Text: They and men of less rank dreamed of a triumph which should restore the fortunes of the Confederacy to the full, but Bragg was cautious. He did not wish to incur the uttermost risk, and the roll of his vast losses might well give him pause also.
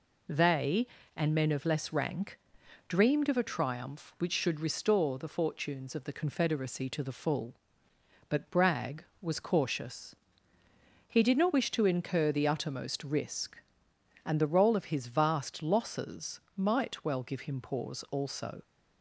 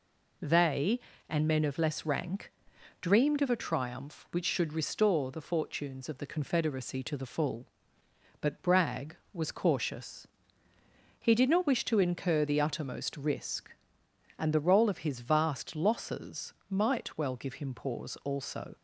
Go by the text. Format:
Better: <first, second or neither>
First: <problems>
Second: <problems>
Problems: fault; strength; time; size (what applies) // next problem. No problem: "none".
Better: neither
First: pauses between "rank" and "dreamed"; noticeable; at 2.3 s; 0.52 s long // pauses between "losses" and "might"; slight; at 16.3 s; 0.16 s long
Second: pauses between "rank" and "dreamed"; noticeable; at 2.4 s; 0.52 s long // pauses between "losses" and "might"; slight; at 16.5 s; 0.16 s long